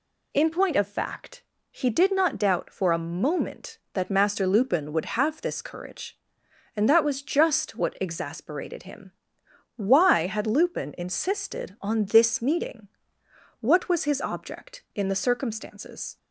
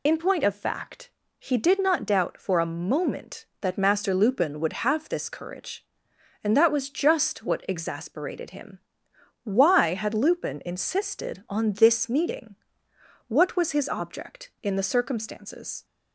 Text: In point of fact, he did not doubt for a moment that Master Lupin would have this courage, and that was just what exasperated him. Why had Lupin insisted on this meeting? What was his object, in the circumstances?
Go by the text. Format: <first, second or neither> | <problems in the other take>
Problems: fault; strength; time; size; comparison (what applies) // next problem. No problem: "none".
first | loses the start of "In"; at 0.0 s; 45 ms